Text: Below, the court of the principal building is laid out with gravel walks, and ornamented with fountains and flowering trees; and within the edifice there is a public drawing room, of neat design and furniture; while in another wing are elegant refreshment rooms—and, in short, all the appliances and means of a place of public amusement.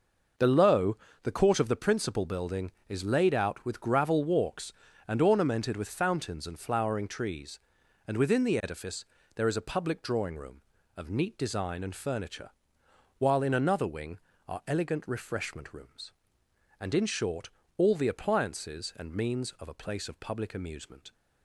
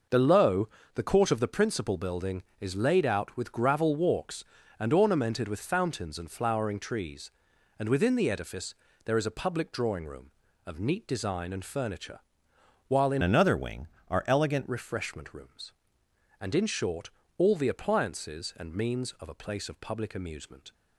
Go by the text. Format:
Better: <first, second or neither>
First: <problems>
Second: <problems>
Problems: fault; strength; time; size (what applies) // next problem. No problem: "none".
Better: first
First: pauses between "edifice" and "there"; slight; at 9.0 s; 0.30 s long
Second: pauses between "edifice" and "there"; slight; at 8.7 s; 0.30 s long // changes voice from "another" to "elegant"; from 13.2 to 14.6 s; 1.4 s long